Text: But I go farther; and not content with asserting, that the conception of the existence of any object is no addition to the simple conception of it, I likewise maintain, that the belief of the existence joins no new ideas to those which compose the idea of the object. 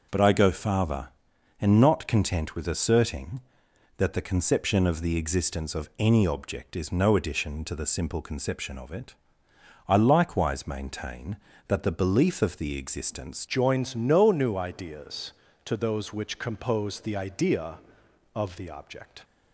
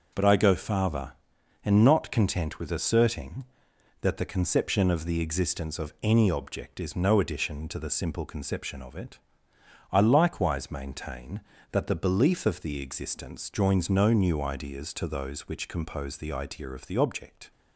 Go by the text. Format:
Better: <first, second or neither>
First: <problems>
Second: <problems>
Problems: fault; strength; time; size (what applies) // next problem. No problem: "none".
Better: second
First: changes voice at "joins"; from 13.4 s on; 5.8 s long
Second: none